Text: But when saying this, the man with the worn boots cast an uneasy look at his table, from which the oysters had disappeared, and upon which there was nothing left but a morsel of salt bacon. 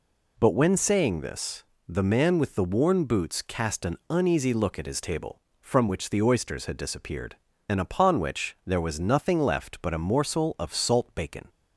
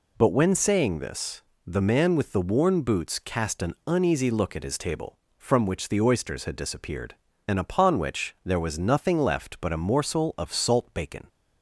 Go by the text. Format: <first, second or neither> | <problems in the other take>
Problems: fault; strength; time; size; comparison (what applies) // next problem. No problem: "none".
neither | none